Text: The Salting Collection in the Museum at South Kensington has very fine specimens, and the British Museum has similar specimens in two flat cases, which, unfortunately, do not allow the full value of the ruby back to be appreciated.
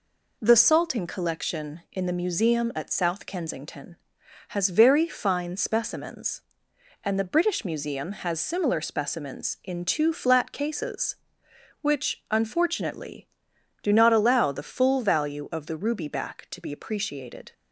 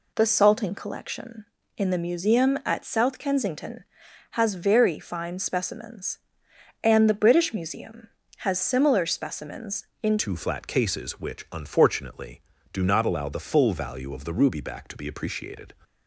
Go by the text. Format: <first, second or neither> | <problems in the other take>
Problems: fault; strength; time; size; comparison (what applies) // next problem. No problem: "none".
first | changes voice at "two"; from 10.1 s on; 5.6 s long